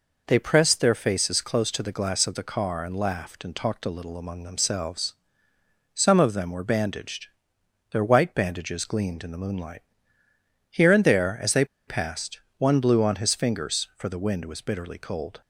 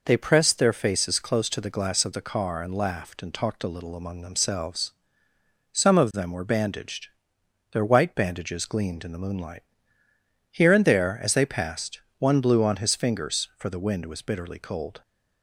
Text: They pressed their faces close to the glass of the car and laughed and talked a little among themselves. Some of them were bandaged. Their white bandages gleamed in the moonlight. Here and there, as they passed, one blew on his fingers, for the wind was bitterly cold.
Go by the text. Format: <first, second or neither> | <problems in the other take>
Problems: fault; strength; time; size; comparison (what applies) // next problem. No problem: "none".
second | pauses between "they" and "passed"; slight; at 11.6 s; 0.22 s long